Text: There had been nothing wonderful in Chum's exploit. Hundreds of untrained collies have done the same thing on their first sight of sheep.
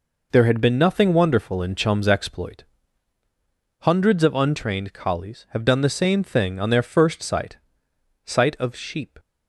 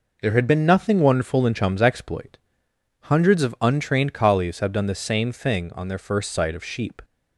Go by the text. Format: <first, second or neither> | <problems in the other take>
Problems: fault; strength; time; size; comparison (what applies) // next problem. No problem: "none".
second | says "sight" twice; at 8.2 s